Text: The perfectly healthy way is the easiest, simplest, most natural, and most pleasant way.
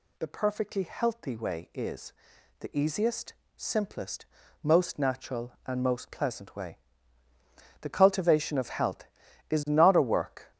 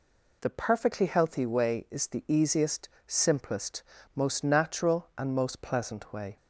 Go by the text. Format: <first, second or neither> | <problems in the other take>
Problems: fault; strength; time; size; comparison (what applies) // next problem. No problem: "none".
second | pauses between "is" and "the"; noticeable; at 2.1 s; 0.46 s long // goes on to say "The cultivation of health is not a work"; strong; from 7.8 s on; 2.6 s long